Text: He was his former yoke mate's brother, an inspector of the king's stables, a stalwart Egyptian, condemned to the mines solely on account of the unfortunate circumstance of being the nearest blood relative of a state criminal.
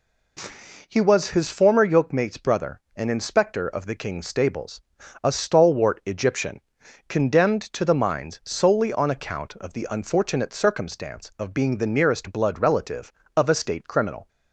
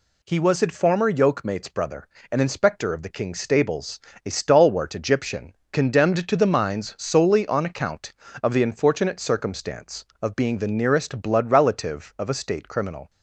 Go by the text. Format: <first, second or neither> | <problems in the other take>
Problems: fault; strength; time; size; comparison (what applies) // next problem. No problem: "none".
neither | none